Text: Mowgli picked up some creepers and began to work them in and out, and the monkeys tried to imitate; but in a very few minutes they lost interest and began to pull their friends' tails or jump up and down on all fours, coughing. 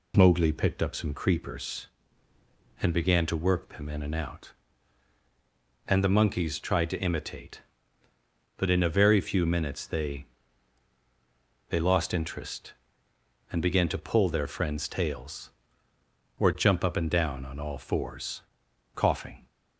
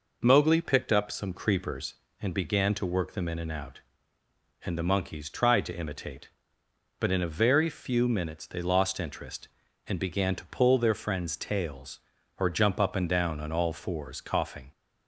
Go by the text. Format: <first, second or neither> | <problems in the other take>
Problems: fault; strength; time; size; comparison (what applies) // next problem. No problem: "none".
second | says "they" twice; at 11.6 s